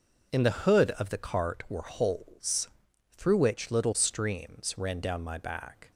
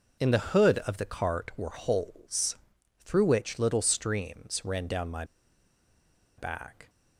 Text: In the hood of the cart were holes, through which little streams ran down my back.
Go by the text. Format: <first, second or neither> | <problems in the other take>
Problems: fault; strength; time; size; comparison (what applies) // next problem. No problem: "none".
first | pauses between "my" and "back"; at 5.2 s; 1.1 s long